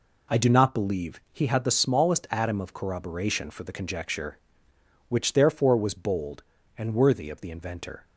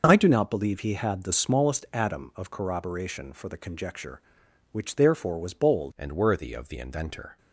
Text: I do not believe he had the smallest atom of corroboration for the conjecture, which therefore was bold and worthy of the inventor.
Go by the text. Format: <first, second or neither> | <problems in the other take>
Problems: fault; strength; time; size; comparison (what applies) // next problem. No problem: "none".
first | changes voice at "and"; from 5.9 s on; 1.4 s long